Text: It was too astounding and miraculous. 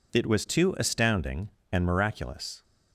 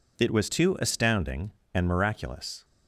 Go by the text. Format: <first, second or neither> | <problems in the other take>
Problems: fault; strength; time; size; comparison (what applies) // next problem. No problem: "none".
neither | none